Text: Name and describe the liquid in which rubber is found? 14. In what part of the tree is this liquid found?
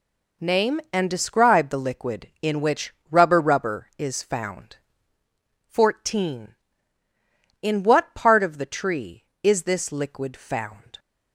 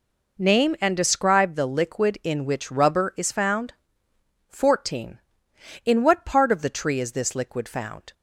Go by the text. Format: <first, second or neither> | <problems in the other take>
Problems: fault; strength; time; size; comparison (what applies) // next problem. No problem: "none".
second | pauses between "which" and "rubber"; slight; at 2.9 s; 0.18 s long // says "rubber" twice; at 3.4 s